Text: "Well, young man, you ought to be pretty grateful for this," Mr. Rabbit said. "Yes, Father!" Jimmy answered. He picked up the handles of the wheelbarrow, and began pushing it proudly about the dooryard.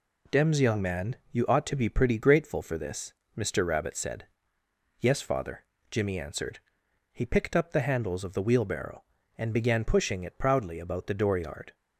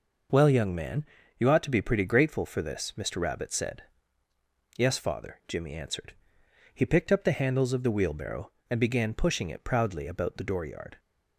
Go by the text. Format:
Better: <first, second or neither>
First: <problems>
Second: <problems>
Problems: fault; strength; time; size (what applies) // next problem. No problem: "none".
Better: second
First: says "Dems" for "Well"; at 0.3 s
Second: none